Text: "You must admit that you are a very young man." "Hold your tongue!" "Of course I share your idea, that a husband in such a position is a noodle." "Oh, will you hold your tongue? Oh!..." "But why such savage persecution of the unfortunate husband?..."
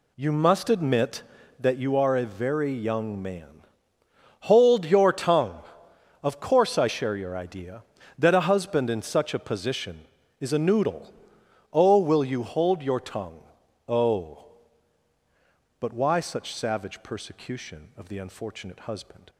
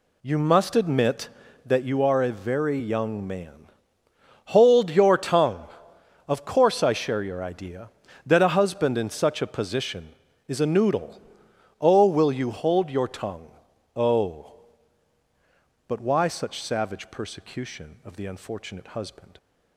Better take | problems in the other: neither | none

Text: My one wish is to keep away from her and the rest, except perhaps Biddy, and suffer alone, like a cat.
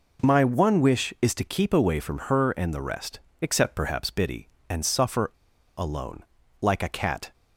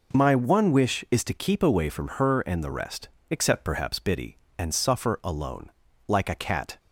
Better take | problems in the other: second | pauses between "suffer" and "alone"; noticeable; at 5.3 s; 0.46 s long

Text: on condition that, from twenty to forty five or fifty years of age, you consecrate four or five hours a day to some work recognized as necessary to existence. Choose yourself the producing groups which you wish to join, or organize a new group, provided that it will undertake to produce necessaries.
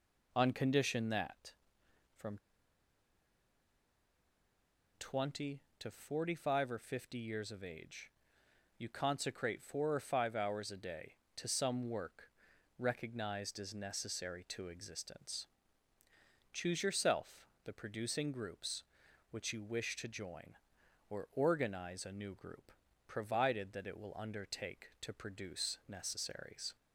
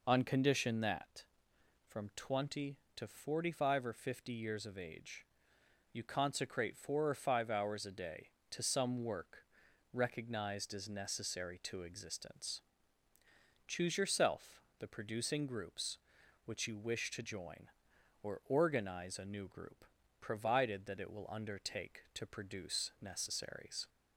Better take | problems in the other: second | pauses between "from" and "twenty"; strong; at 2.3 s; 2.6 s long // pauses between "work" and "recognized"; noticeable; at 12.2 s; 0.48 s long; noticeable in the second // pauses between "yourself" and "the"; slight; at 17.4 s; 0.18 s long; slight in the second

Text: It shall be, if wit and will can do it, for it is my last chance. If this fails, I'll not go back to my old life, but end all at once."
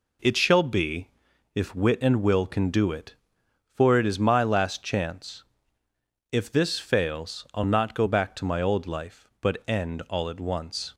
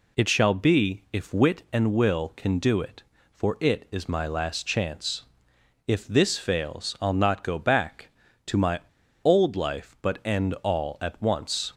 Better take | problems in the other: first | pauses between "my" and "old"; at 8.8 s; 0.43 s long

